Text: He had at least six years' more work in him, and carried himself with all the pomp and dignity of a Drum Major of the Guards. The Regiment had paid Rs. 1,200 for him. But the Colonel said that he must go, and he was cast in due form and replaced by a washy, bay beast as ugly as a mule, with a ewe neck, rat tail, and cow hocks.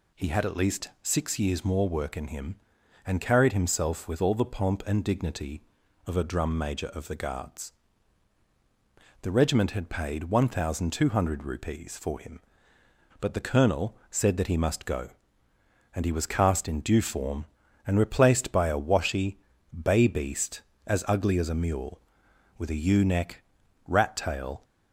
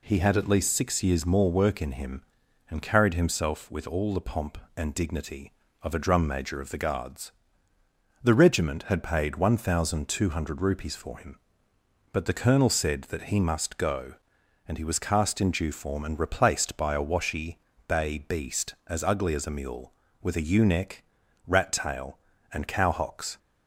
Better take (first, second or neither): second